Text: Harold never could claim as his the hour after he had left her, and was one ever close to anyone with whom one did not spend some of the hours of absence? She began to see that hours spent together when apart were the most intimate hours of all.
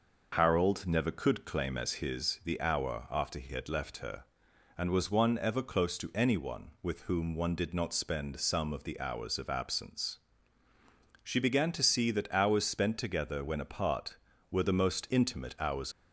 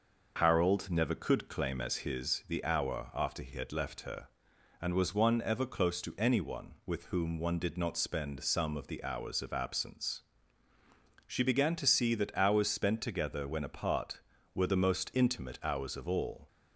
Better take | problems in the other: second | stops before "of all"; at 15.9 s

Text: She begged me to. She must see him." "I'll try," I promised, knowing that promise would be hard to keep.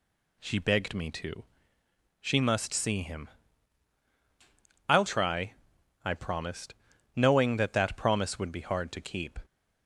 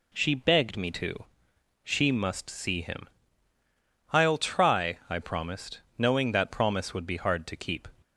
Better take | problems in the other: second | says "that" twice; at 7.7 s

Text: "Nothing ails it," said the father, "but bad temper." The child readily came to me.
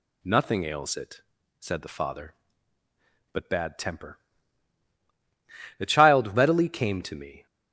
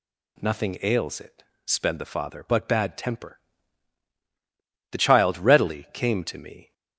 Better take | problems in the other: first | says "sped" for "said"; at 1.6 s

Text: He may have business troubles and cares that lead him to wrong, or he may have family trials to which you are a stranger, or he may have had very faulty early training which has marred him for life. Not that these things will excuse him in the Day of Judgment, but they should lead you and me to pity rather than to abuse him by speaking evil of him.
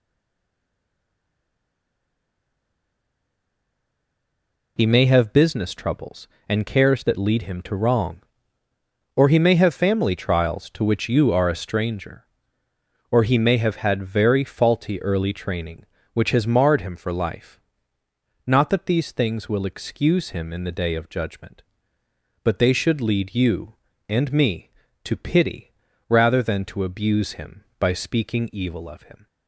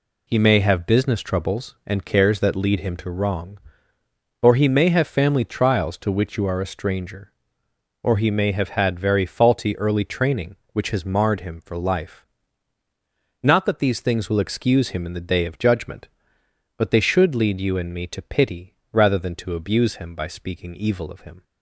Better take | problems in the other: second | stays silent before the first word; strong; until 4.7 s; 4.7 s long // pauses between "pity" and "rather"; at 25.7 s; 0.40 s long; slight in the second

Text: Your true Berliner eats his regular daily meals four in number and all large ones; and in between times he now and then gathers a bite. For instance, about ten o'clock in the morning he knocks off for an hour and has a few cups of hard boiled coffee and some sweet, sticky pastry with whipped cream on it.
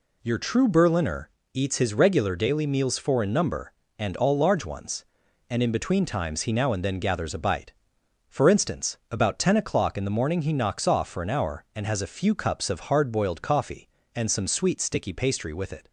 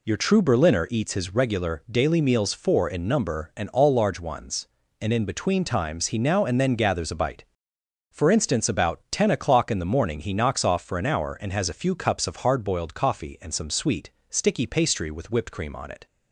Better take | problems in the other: second | pauses between "Berliner" and "eats"; slight; at 1.3 s; 0.24 s long // skips "whipped cream on"; at 15.7 s

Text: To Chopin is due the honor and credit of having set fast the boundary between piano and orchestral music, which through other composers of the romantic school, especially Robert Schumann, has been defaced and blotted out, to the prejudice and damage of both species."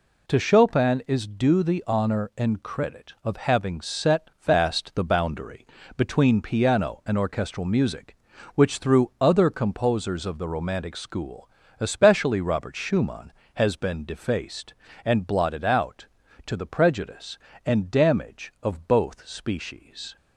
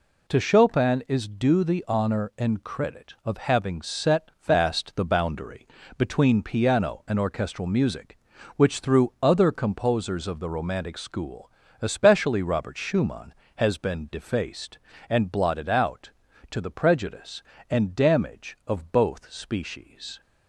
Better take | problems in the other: neither | pauses between "boundary" and "between"; slight; the same in both

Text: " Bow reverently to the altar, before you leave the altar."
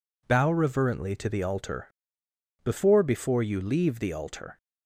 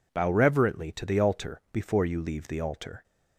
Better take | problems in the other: second | says "before" twice; at 3.0 s

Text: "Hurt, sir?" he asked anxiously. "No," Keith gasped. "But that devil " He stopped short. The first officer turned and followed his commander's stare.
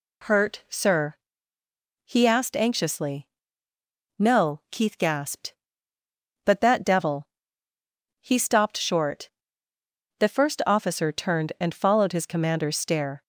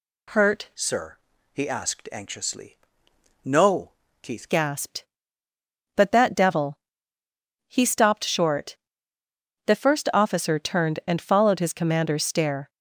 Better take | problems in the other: first | changes voice from "sir" to "Keith"; from 0.7 to 4.4 s; 3.7 s long

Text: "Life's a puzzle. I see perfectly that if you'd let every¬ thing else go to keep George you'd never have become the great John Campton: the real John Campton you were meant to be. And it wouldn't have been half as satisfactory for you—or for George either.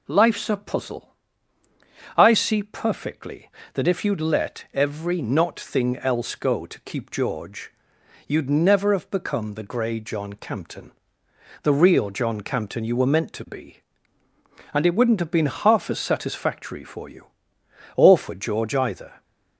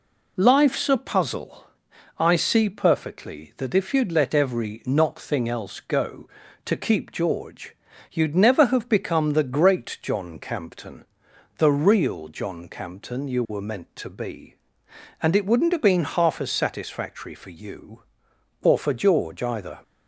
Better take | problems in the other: second | pauses between "George" and "you'd"; noticeable; at 7.6 s; 0.56 s long; also in the second // says "grey" for "great"; at 9.6 s

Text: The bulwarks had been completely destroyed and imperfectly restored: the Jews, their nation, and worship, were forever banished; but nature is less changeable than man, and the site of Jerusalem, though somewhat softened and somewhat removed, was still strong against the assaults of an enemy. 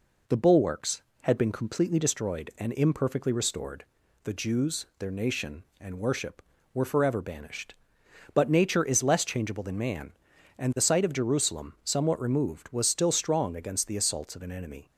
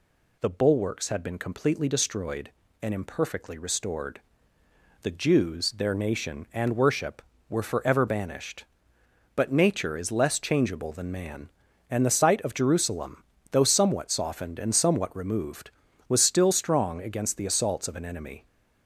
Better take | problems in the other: second | skips "though somewhat softened and"; at 11.7 s

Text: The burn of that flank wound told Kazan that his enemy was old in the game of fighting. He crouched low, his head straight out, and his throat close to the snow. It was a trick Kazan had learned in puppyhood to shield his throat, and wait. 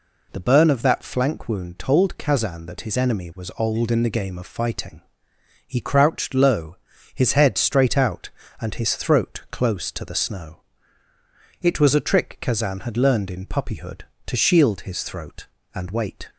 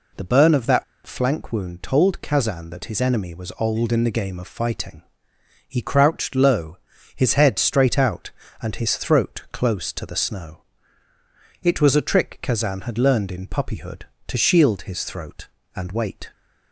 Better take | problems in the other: first | pauses between "that" and "flank"; slight; at 0.8 s; 0.21 s long

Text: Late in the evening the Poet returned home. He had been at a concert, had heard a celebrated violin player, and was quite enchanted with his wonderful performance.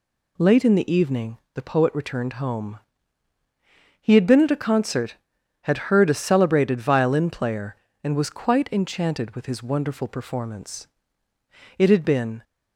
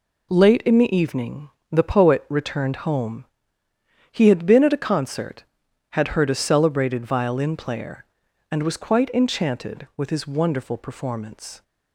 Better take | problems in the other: second | pauses between "evening" and "the"; slight; at 1.3 s; 0.16 s long; slight in the second // goes on to say "It had been"; noticeable; from 11.7 s on; 0.66 s long

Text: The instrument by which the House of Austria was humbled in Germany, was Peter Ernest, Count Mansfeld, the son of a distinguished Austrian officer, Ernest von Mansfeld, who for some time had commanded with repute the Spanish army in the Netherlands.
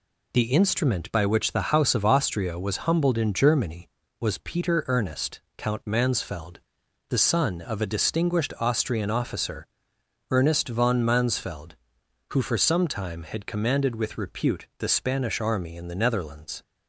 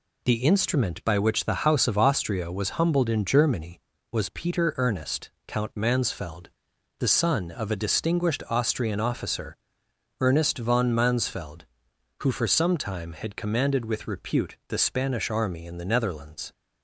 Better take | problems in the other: neither | none

